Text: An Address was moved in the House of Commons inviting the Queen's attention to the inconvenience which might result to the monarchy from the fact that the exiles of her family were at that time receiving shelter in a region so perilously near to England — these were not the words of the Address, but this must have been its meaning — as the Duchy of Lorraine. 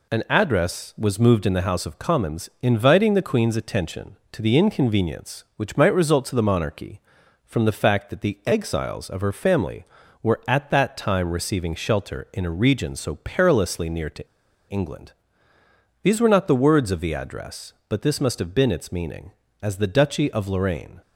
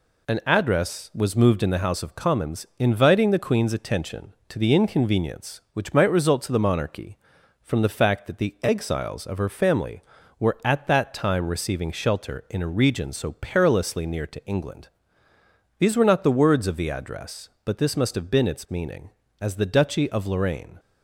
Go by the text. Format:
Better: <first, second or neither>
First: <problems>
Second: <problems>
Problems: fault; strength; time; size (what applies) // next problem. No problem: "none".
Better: second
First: pauses between "to" and "England"; at 14.2 s; 0.44 s long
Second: none